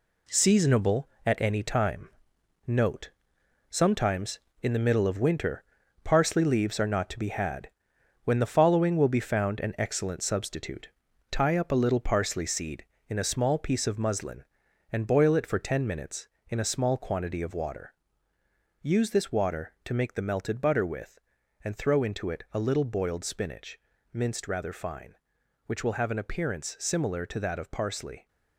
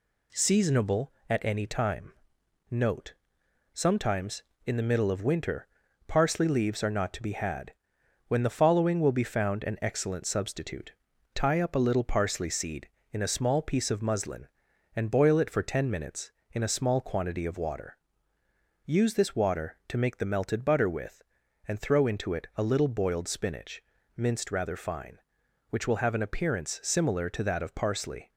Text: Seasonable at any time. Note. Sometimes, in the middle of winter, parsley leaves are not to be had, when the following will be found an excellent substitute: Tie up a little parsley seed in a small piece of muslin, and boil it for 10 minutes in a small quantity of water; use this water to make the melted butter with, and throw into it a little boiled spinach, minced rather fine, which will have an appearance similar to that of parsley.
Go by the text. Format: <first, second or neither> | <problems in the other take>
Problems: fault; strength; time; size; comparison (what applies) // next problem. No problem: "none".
second | gets quieter; strong; throughout; 7 dB